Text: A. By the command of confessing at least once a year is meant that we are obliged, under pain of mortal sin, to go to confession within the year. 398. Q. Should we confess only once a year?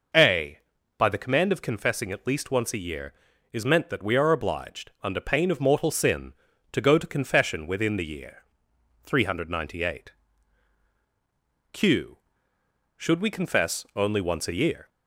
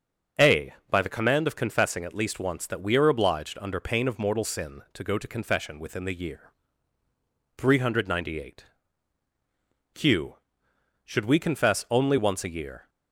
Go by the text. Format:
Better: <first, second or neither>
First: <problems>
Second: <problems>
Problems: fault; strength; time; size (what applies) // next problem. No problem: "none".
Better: first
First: none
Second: starts louder than the rest; until 1.5 s; 6.5 dB // skips "a year is meant"; at 2.6 s